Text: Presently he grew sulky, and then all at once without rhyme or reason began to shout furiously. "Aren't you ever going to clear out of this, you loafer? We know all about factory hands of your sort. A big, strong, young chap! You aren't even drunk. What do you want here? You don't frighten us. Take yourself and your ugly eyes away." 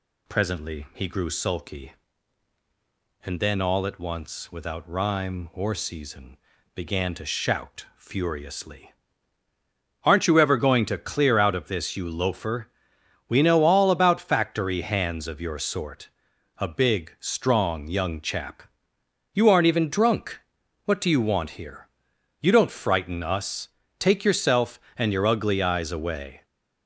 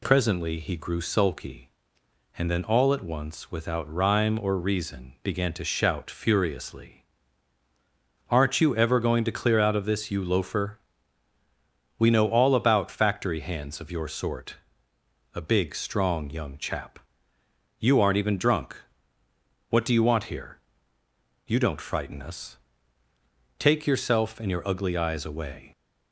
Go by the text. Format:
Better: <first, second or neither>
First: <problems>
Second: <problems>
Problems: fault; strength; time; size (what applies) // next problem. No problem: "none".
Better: second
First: says "season" for "reason"; at 5.7 s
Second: none